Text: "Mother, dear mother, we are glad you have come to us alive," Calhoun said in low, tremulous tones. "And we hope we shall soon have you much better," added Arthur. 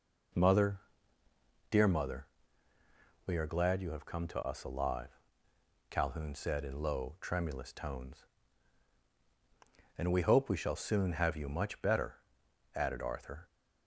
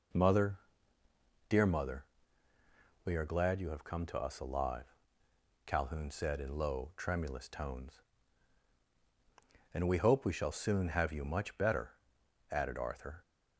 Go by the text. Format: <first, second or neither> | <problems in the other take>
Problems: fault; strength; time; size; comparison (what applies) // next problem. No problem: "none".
neither | none